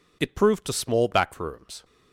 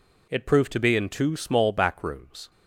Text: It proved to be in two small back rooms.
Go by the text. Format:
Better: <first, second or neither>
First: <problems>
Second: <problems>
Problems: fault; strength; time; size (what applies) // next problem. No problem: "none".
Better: second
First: skips "be in two"; at 0.7 s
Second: none